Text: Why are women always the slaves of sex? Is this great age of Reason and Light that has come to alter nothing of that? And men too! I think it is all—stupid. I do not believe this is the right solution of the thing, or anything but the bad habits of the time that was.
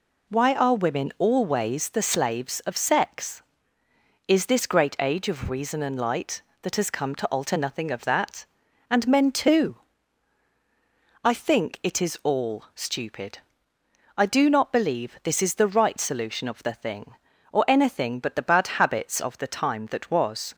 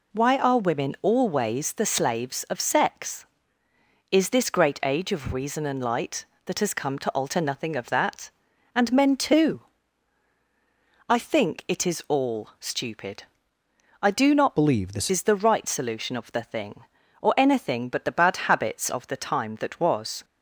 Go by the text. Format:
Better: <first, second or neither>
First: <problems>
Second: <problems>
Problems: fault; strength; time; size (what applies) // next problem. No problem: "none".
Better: first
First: none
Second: changes voice from "believe" to "this"; from 14.5 to 15.0 s; 0.5 s long